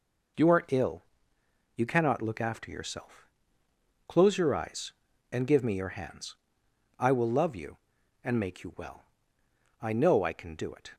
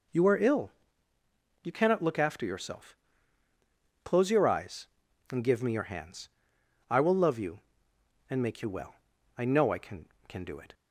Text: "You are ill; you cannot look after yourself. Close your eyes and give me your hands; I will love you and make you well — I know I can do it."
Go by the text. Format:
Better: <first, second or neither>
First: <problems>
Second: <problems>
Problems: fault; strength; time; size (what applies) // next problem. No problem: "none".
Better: first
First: none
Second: says "can" twice; at 10.2 s